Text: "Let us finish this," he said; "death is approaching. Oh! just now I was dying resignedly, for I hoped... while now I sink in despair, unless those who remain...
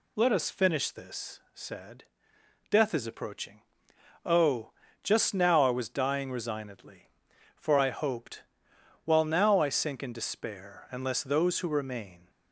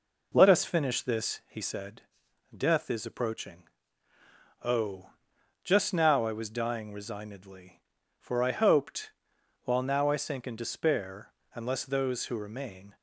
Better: second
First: skips "he"; at 1.4 s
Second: none

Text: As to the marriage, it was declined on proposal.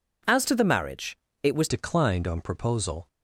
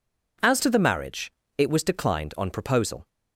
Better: second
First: changes voice at "declined"; from 1.6 s on; 1.4 s long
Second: none

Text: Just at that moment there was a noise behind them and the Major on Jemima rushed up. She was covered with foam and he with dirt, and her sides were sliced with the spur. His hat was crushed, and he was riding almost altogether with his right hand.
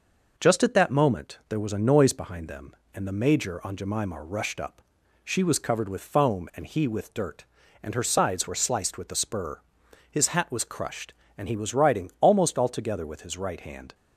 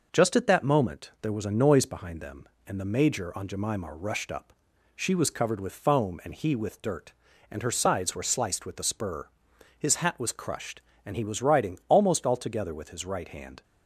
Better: neither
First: none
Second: none

